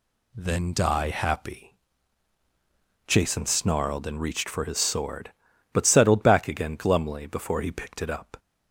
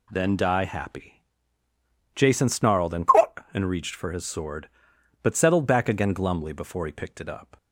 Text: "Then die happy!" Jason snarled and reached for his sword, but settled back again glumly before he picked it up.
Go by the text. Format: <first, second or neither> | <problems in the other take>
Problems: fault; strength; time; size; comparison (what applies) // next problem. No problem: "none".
first | says "and" twice; at 3.5 s